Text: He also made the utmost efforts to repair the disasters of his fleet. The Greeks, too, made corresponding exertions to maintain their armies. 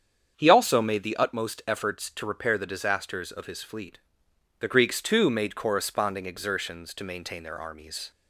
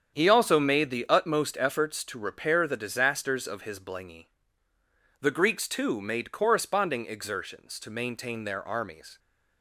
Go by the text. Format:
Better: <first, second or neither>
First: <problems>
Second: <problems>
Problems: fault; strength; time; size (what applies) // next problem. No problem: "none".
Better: first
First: starts louder than the rest; strong; until 1.3 s; 7.5 dB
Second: starts louder than the rest; strong; until 1.1 s; 8 dB // says "blingy" for "fleet"; at 3.8 s